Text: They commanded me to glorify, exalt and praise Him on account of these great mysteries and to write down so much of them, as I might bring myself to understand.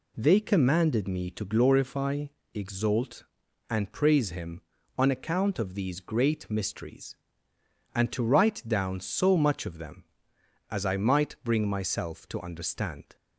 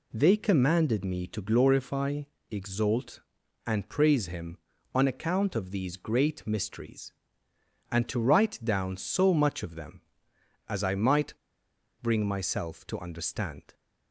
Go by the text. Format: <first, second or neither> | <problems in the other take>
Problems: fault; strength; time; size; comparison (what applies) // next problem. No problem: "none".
first | pauses between "might" and "bring"; noticeable; at 11.3 s; 0.68 s long